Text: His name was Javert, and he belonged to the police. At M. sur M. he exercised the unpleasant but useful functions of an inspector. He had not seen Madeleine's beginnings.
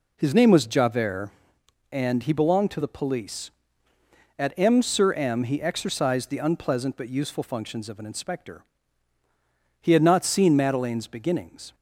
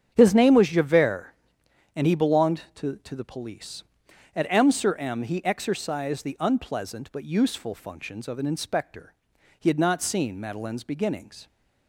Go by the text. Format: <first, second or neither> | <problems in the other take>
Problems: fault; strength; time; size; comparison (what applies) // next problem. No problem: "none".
first | starts louder than the rest; strong; until 1.1 s; 8 dB // says "to" twice; at 2.9 s